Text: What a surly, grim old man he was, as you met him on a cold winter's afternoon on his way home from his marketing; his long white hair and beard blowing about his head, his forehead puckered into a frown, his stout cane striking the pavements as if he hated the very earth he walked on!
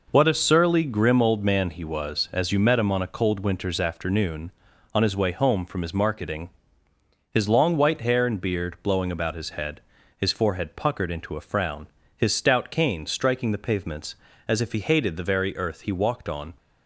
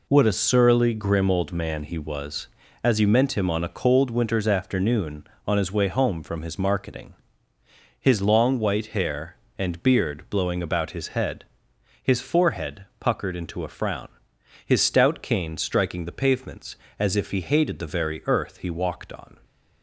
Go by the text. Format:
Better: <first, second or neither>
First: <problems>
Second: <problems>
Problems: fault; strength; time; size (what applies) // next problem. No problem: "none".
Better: first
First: none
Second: says "meant" for "met"; at 3.0 s